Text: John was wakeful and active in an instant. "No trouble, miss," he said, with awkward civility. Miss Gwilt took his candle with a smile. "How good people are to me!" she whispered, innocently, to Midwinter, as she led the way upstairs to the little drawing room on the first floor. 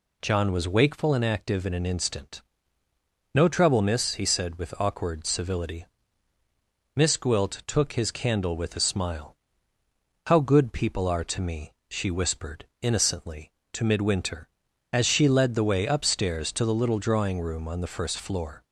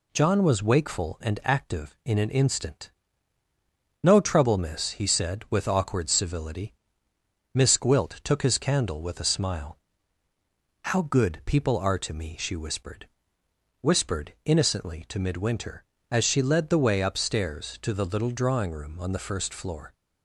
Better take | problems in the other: first | says "whispered" twice; at 13.8 s

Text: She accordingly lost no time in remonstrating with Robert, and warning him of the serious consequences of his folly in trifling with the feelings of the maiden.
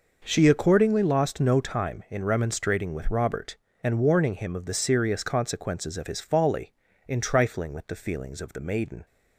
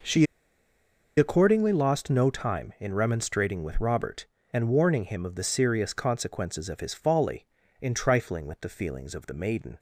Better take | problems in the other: first | pauses between "She" and "accordingly"; noticeable; at 0.2 s; 0.91 s long

